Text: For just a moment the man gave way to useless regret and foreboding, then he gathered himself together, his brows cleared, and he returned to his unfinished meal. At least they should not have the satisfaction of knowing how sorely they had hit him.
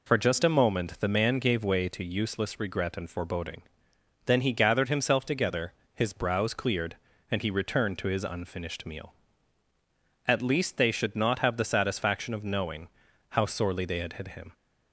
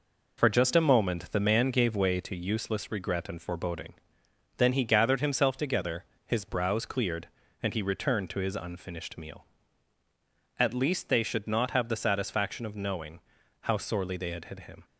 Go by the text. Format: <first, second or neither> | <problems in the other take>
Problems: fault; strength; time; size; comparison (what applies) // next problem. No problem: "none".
first | gets quieter; noticeable; throughout; 5 dB // pauses between "knowing" and "how"; at 13.1 s; 0.44 s long; also in the first